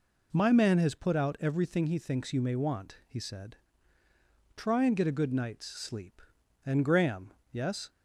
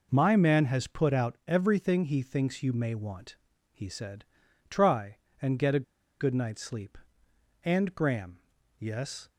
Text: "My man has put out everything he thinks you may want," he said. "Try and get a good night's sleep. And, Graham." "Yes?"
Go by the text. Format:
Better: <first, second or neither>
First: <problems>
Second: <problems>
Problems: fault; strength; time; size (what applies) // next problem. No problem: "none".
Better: first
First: none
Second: pauses between "a" and "good"; slight; at 5.8 s; 0.35 s long